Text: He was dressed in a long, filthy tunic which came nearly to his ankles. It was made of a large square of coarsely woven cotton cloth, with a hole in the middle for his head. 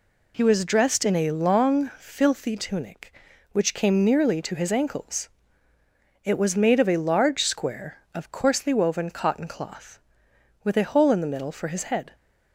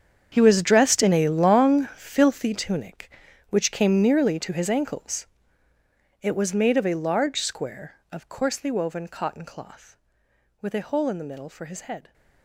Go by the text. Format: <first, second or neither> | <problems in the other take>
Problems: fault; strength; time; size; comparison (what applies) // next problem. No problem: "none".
first | gets quieter; strong; throughout; 16.5 dB